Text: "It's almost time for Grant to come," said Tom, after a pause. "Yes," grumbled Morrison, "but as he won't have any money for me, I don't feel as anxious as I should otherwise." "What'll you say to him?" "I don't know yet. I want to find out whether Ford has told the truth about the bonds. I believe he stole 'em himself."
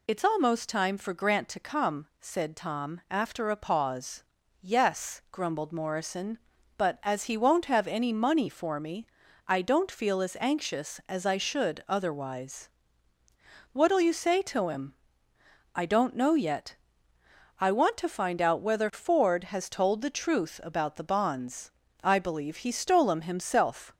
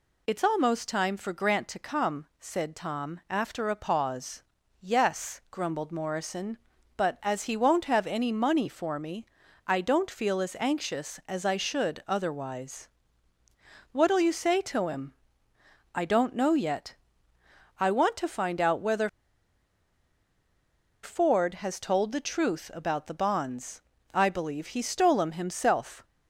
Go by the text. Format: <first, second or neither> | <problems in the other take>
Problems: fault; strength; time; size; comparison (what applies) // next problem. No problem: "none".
first | pauses between "whether" and "Ford"; strong; at 19.0 s; 1.9 s long